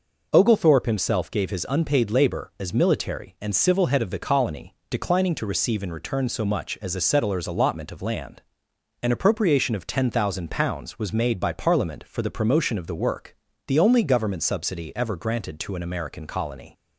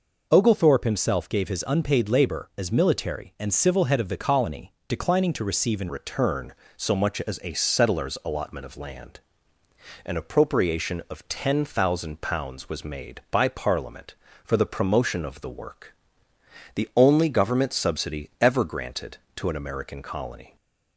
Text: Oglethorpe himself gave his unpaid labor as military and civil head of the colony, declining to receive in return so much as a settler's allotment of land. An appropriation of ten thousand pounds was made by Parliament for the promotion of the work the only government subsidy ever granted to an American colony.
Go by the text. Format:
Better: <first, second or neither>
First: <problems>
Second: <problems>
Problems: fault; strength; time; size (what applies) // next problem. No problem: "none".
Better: first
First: pauses between "work" and "the"; slight; at 13.3 s; 0.32 s long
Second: changes voice at "return"; from 5.8 s on; 14.7 s long // pauses between "work" and "the"; noticeable; at 15.9 s; 0.82 s long